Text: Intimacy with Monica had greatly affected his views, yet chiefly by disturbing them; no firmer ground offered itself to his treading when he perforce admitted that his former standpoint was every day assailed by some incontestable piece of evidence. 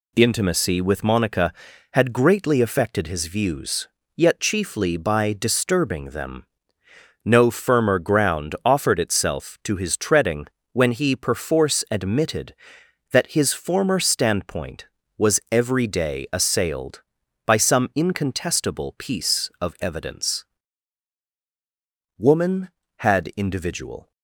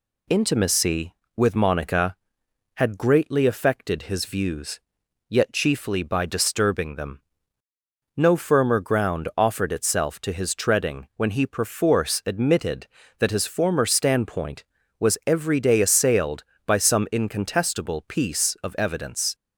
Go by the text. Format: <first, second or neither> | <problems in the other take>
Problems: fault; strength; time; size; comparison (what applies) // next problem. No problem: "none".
second | pauses between "treading" and "when"; slight; at 10.4 s; 0.26 s long // goes on to say "Woman had individual"; strong; from 22.1 s on; 1.9 s long